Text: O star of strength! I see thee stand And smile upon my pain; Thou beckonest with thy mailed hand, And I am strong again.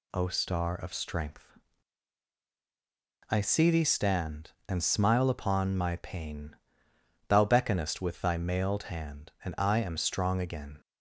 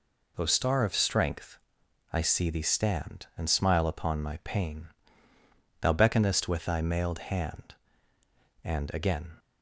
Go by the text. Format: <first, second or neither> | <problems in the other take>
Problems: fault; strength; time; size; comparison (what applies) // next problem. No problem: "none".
first | skips "I am strong"; at 8.9 s